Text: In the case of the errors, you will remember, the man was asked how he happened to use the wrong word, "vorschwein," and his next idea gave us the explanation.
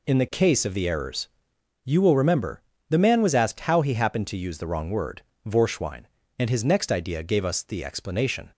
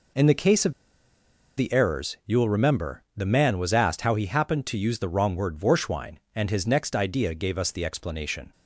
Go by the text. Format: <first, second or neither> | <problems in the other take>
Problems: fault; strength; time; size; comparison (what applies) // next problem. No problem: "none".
first | pauses between "of" and "the"; noticeable; at 0.7 s; 0.86 s long